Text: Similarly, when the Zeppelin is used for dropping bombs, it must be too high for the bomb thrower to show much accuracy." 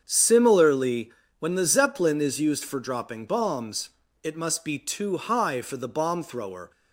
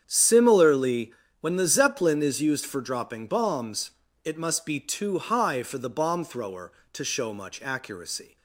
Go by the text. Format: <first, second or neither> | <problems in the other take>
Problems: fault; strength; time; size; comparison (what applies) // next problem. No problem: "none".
second | starts louder than the rest; strong; until 1.0 s; 7.5 dB; strong in the second // stops before "to show much accuracy"; at 6.7 s